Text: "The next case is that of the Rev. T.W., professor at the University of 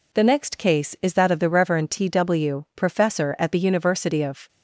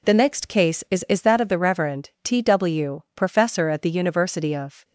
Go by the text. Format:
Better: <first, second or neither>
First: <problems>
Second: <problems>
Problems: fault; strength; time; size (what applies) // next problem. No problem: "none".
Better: first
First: none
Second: says "is" twice; at 1.0 s